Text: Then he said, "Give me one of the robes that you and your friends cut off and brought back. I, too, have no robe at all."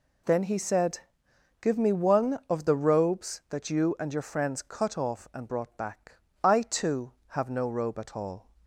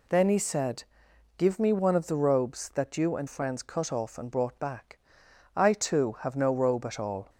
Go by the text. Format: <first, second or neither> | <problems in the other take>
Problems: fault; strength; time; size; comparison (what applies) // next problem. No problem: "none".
first | skips "your"; at 3.2 s